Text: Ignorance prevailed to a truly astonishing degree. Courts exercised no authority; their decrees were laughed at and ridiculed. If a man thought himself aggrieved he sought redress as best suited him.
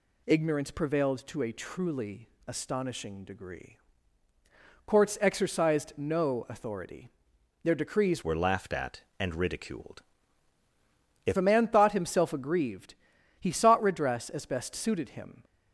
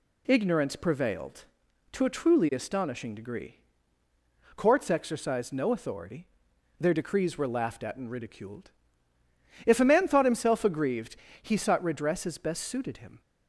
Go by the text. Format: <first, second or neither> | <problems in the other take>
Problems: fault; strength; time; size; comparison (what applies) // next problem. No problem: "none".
second | pauses between "truly" and "astonishing"; slight; at 2.2 s; 0.18 s long // changes voice from "were" to "If"; from 8.2 to 11.3 s; 3.1 s long // pauses between "aggrieved" and "he"; at 12.9 s; 0.44 s long; slight in the second